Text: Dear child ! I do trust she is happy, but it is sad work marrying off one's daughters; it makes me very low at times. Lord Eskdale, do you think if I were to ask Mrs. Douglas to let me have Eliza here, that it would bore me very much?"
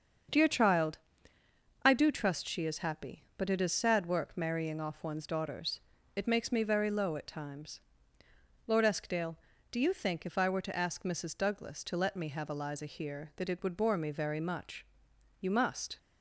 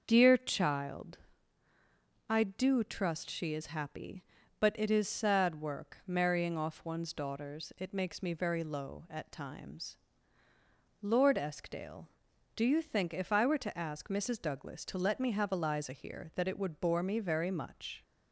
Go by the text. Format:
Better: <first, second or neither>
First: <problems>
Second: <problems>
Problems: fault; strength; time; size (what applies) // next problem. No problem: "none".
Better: second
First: starts louder than the rest; until 2.1 s; 7 dB // goes on to say "You must"; from 15.3 s on; 0.58 s long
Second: starts louder than the rest; until 1.0 s; 6.5 dB